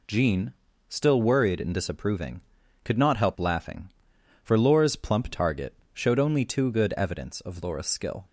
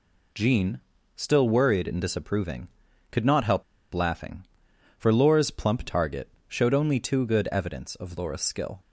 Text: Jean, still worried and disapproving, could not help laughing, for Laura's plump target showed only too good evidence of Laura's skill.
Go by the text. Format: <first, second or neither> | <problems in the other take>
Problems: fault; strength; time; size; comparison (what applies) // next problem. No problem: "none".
first | pauses between "help" and "laughing"; slight; at 3.6 s; 0.31 s long // pauses between "target" and "showed"; slight; at 6.2 s; 0.20 s long; slight in the first